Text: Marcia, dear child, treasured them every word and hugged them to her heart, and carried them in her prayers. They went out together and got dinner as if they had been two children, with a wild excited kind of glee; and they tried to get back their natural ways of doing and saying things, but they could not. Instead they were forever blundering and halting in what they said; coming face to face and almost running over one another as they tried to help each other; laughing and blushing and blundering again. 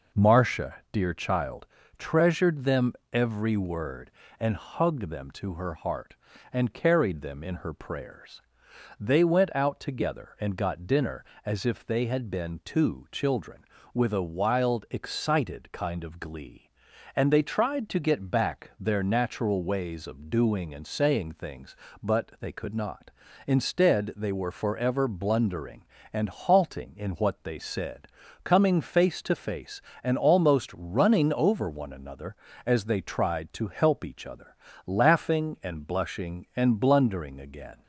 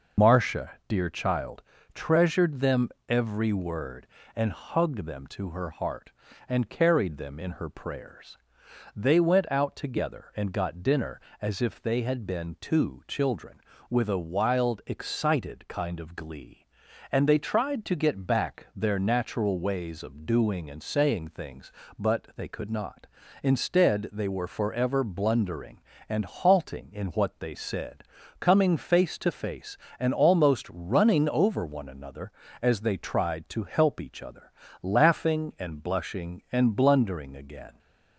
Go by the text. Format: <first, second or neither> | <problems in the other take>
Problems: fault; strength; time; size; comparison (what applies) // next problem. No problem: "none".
first | loses the start of "Marcia"; at 0.1 s; 80 ms // pauses between "them" and "every"; slight; at 2.8 s; 0.22 s long; slight in the first